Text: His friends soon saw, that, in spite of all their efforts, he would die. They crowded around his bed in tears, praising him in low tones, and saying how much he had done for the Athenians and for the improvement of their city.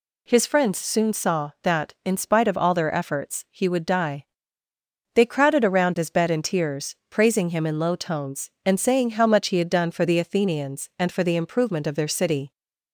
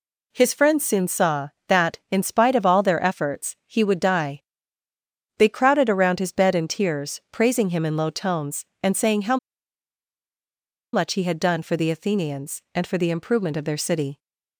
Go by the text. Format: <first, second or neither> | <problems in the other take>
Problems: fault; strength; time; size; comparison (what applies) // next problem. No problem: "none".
first | pauses between "how" and "much"; strong; at 9.3 s; 1.5 s long